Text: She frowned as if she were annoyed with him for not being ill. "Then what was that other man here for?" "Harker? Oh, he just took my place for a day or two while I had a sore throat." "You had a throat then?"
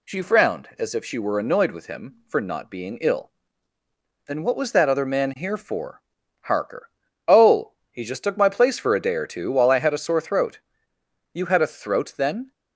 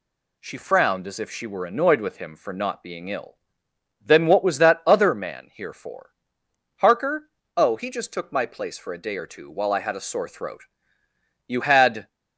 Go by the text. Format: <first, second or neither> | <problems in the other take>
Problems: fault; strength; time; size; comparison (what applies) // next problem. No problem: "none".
first | stops before "a throat then"; at 12.0 s